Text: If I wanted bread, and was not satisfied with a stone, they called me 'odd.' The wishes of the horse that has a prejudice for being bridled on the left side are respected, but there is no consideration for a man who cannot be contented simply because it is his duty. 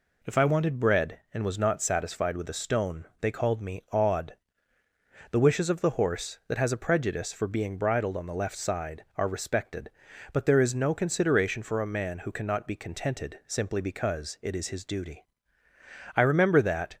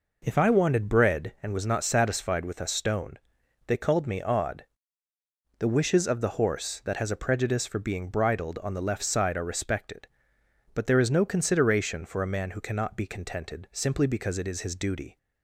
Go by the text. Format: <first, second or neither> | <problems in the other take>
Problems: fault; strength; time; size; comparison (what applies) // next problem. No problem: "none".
second | goes on to say "I remember that"; noticeable; from 16.1 s on; 0.82 s long